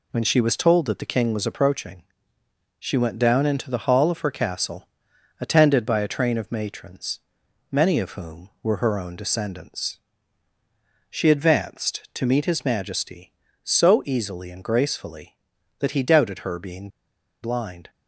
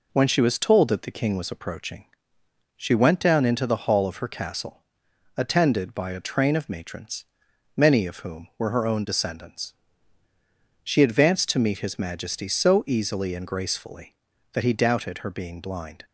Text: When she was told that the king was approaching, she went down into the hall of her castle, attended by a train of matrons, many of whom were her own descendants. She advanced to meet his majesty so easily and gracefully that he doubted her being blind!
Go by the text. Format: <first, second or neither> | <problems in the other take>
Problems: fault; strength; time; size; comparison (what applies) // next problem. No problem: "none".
second | pauses between "being" and "blind"; noticeable; at 16.8 s; 0.54 s long